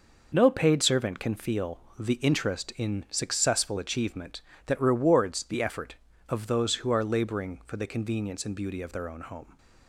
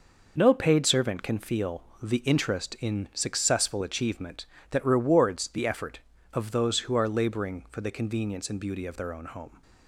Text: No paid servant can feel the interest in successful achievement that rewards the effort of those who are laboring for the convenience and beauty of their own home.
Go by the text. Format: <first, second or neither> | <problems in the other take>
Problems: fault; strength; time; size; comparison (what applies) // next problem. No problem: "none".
neither | pauses between "feel" and "the"; slight; the same in both